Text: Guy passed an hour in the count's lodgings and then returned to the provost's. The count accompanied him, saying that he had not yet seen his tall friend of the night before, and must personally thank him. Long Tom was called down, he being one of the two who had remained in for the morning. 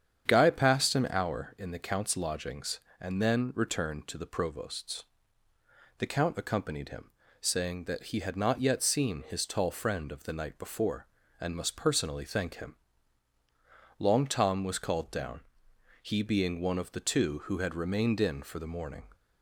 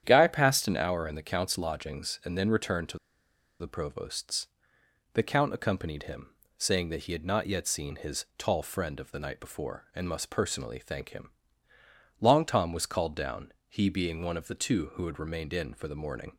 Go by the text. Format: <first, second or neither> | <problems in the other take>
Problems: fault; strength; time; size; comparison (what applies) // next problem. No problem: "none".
first | starts louder than the rest; strong; until 1.0 s; 9.5 dB; strong in the first // pauses between "to" and "the"; noticeable; at 2.9 s; 0.62 s long